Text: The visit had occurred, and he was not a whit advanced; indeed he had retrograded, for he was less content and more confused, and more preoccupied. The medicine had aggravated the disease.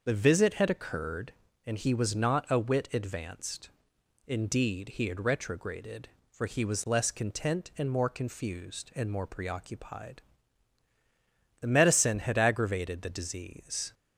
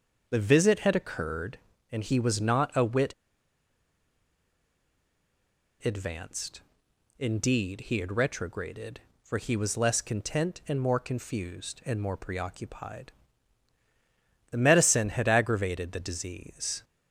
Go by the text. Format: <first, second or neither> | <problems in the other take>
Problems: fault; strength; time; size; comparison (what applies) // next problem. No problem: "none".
first | starts louder than the rest; until 1.3 s; 6.5 dB; also in the first // pauses between "whit" and "advanced"; strong; at 3.1 s; 2.7 s long